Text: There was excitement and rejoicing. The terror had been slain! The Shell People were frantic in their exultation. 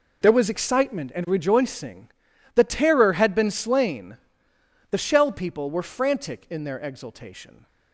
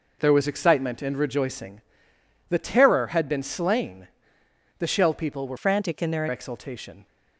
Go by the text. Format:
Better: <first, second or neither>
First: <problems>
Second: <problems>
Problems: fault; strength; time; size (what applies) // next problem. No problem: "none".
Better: first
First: none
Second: changes voice from "frantic" to "their"; from 5.5 to 6.2 s; 0.7 s long